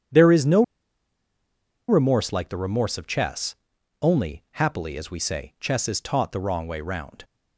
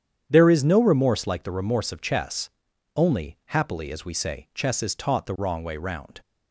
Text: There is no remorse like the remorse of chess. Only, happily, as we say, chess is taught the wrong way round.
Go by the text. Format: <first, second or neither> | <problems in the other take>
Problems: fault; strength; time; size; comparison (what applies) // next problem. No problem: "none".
second | starts louder than the rest; strong; until 2.3 s; 9 dB; strong in the second // pauses between "no" and "remorse"; strong; at 0.6 s; 1.2 s long